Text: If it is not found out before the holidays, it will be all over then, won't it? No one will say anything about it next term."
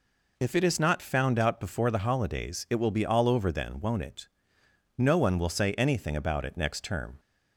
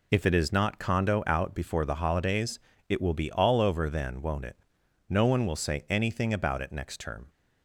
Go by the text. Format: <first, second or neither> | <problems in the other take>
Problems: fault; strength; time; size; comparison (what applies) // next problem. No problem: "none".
first | says "condo" for "found"; at 0.7 s